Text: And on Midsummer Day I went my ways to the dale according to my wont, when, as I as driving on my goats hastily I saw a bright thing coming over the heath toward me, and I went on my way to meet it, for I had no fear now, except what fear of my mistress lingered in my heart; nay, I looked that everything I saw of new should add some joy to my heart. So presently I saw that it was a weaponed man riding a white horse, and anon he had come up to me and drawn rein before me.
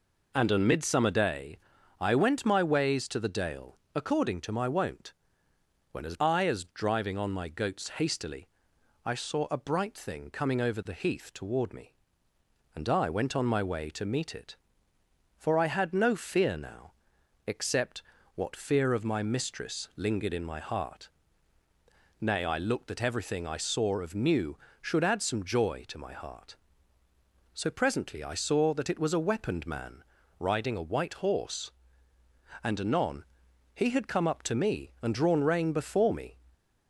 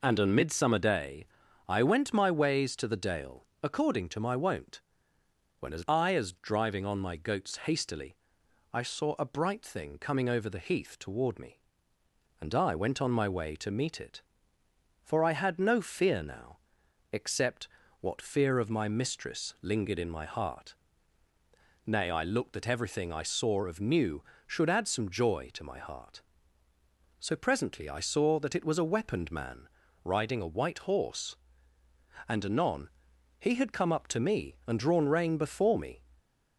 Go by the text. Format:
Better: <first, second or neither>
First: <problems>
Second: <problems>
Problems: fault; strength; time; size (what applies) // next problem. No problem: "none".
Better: neither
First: pauses between "Day" and "I"; at 1.5 s; 0.40 s long // pauses between "dale" and "according"; slight; at 3.7 s; 0.18 s long // pauses between "hastily" and "I"; noticeable; at 8.4 s; 0.58 s long // pauses between "except" and "what"; slight; at 18.0 s; 0.32 s long // pauses between "man" and "riding"; slight; at 30.0 s; 0.34 s long // pauses between "anon" and "he"; noticeable; at 33.2 s; 0.50 s long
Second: pauses between "Day" and "I"; at 1.2 s; 0.40 s long // pauses between "dale" and "according"; slight; at 3.4 s; 0.18 s long // pauses between "hastily" and "I"; noticeable; at 8.1 s; 0.58 s long // pauses between "except" and "what"; slight; at 17.6 s; 0.32 s long // pauses between "man" and "riding"; slight; at 29.6 s; 0.34 s long // pauses between "anon" and "he"; noticeable; at 32.8 s; 0.50 s long